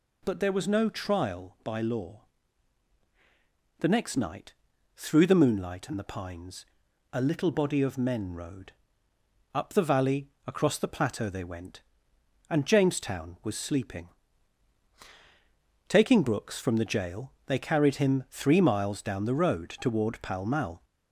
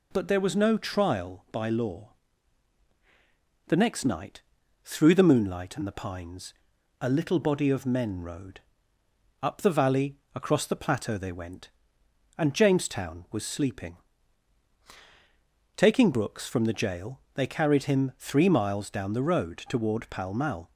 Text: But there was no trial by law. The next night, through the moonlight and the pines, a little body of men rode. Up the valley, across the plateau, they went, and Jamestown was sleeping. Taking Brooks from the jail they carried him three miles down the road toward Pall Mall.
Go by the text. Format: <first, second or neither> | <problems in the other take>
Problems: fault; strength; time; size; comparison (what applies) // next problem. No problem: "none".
second | gets louder; slight; throughout; 2 dB